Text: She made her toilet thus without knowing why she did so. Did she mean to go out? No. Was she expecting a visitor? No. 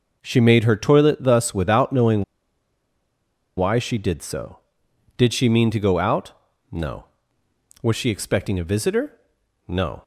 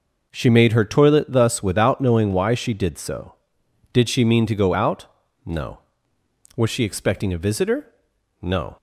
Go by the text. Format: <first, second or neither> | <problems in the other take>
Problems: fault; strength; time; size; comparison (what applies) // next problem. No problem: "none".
second | pauses between "knowing" and "why"; strong; at 2.2 s; 1.3 s long